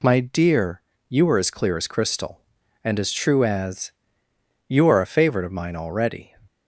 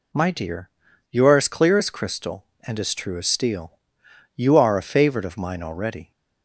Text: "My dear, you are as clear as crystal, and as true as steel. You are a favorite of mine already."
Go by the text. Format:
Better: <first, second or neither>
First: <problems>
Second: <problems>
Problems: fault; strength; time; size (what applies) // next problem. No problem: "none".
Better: second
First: skips "steel"; at 4.2 s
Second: none